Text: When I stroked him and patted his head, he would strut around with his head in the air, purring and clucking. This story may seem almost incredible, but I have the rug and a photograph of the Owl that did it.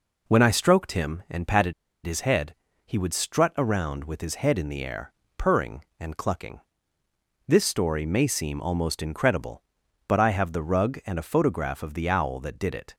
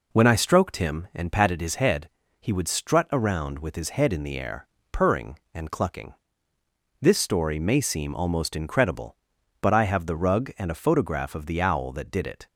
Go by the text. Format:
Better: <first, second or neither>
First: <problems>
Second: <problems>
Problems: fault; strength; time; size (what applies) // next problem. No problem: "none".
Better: second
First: pauses between "patted" and "his"; slight; at 1.7 s; 0.33 s long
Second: none